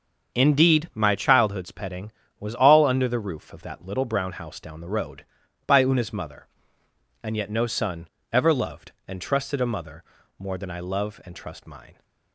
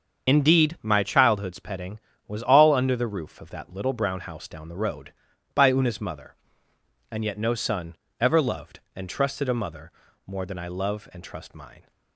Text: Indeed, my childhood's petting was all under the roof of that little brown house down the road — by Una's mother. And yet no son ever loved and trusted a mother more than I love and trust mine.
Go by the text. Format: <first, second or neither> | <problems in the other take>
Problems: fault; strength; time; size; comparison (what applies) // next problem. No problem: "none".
first | loses the start of "Indeed"; at 0.2 s; 50 ms // starts louder than the rest; until 1.3 s; 7 dB; also in the first // pauses between "son" and "ever"; slight; at 7.9 s; 0.24 s long; slight in the first // pauses between "mother" and "more"; slight; at 9.9 s; 0.36 s long; slight in the first